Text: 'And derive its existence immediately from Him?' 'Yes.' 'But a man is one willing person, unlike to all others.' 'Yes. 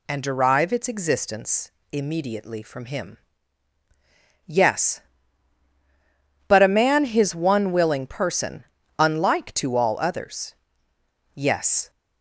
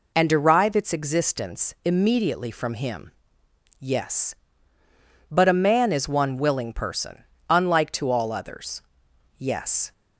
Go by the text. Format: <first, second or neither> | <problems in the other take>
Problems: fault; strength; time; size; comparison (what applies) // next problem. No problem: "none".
second | pauses between "existence" and "immediately"; slight; at 1.6 s; 0.22 s long // says "his" for "is"; at 7.0 s